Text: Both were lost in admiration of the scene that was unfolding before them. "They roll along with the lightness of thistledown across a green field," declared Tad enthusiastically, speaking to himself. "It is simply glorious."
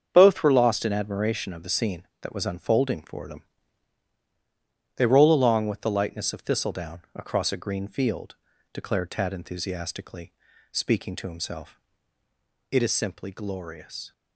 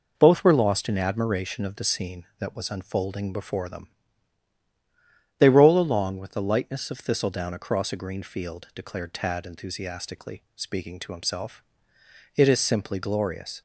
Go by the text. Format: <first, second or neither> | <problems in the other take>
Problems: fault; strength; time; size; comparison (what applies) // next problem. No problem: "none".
second | starts louder than the rest; strong; until 1.1 s; 7.5 dB // says "for" for "before"; at 3.0 s